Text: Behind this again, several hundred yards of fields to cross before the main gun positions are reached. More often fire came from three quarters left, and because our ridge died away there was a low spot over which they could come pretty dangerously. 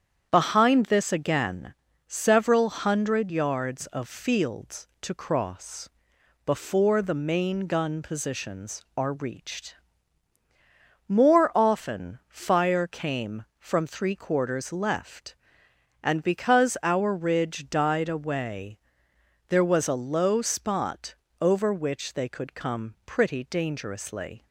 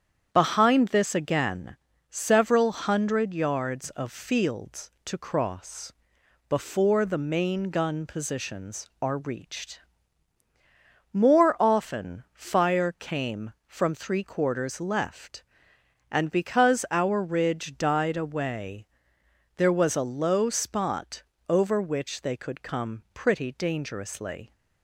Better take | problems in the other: neither | starts louder than the rest; strong; the same in both // pauses between "cross" and "before"; noticeable; the same in both // pauses between "away" and "there"; noticeable; the same in both // pauses between "spot" and "over"; slight; the same in both

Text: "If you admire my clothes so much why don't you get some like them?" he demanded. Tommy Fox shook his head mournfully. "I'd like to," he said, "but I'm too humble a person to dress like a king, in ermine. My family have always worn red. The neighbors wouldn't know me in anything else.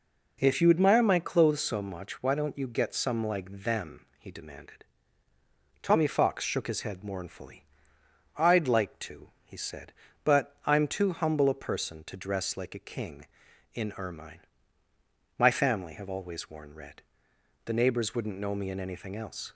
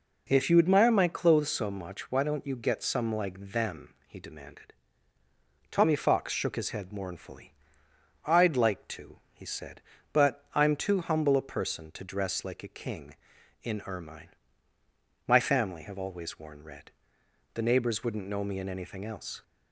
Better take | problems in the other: neither | none

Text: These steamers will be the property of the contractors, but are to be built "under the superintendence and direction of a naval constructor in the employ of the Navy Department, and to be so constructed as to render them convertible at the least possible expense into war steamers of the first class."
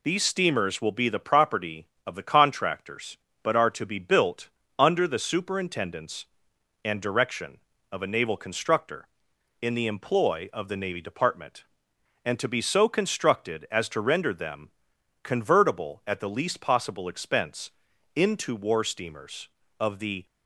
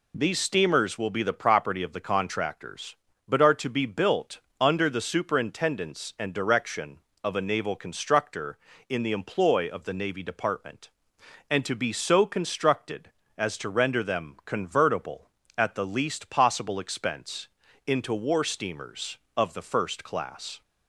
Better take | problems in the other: second | pauses between "built" and "under"; slight; at 4.4 s; 0.30 s long; slight in the second // pauses between "them" and "convertible"; noticeable; at 14.7 s; 0.50 s long // pauses between "expense" and "into"; noticeable; at 17.6 s; 0.46 s long; slight in the second // stops before "first class"; at 20.2 s

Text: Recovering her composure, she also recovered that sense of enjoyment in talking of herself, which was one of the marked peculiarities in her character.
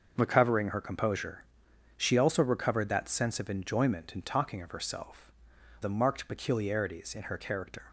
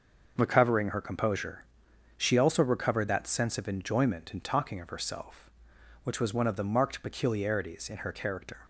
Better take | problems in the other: second | starts louder than the rest; until 1.1 s; 6.5 dB; also in the second // skips "which was one of"; at 5.5 s

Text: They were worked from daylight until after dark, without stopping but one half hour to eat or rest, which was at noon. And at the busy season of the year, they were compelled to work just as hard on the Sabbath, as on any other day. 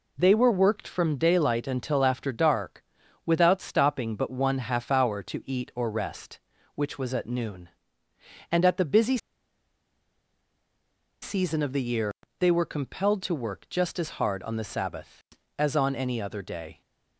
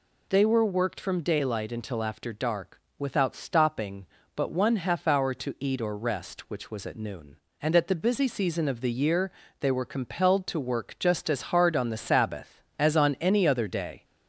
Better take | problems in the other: second | pauses between "busy" and "season"; strong; at 9.1 s; 2.0 s long

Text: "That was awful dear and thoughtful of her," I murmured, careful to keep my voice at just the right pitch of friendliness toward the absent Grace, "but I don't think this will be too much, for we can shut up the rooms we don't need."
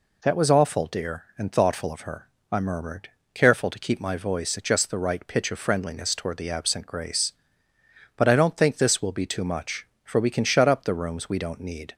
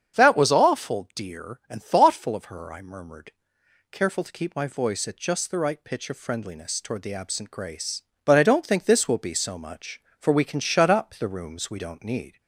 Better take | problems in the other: first | starts louder than the rest; strong; until 1.2 s; 7.5 dB // says "so" for "too"; at 9.3 s

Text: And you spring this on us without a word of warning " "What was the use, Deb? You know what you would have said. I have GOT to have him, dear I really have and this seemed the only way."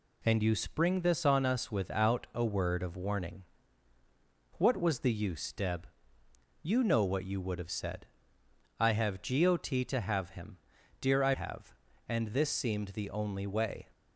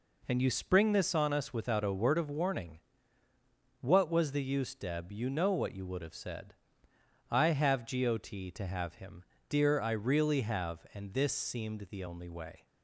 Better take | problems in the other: second | skips "really"; at 11.3 s

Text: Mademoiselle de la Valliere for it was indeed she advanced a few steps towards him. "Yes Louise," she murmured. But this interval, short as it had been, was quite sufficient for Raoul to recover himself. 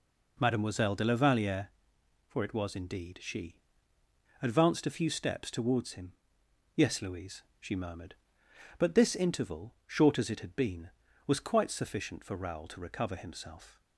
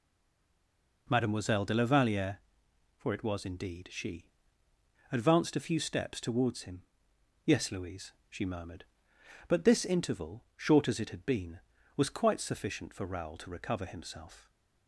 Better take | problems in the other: first | stays silent before the first word; until 1.0 s; 1.0 s long // pauses between "she" and "advanced"; noticeable; at 4.2 s; 0.86 s long; noticeable in the first

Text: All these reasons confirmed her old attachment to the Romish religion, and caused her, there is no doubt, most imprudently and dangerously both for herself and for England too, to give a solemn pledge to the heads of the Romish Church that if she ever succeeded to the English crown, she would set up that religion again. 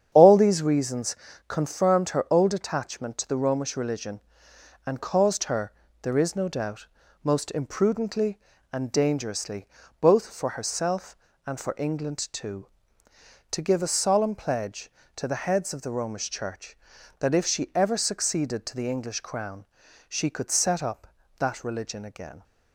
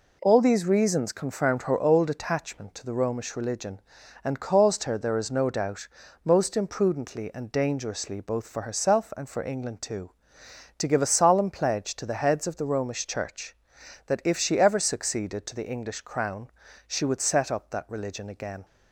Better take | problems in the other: second | starts louder than the rest; strong; until 1.1 s; 8.5 dB // pauses between "reasons" and "confirmed"; slight; at 1.1 s; 0.32 s long // pauses between "dangerously" and "both"; slight; at 9.6 s; 0.36 s long // says "could" for "would"; at 20.2 s

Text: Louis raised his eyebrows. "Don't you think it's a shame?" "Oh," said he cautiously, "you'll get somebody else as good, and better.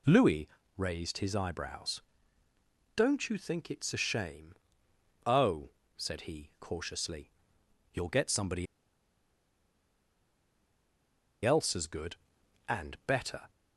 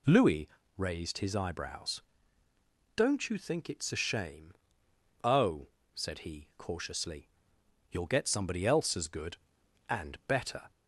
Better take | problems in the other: second | pauses between "Louis" and "raised"; slight; at 0.4 s; 0.28 s long; slight in the second // pauses between "somebody" and "else"; strong; at 8.6 s; 2.7 s long

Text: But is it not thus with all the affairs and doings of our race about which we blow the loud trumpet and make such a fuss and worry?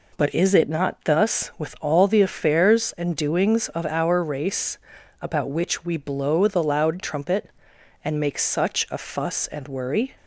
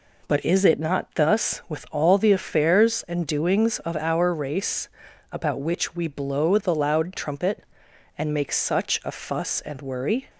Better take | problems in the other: neither | pauses between "race" and "about"; the same in both

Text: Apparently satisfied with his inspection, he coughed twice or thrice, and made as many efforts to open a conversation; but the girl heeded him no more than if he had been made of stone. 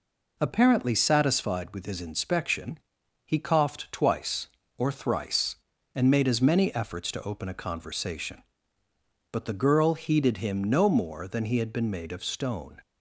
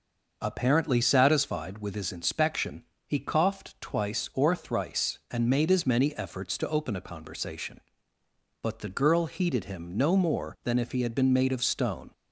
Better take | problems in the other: second | skips "if"; at 11.4 s

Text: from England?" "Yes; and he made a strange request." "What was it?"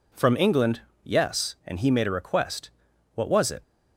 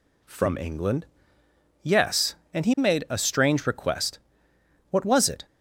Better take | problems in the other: second | skips "strange"; at 2.0 s

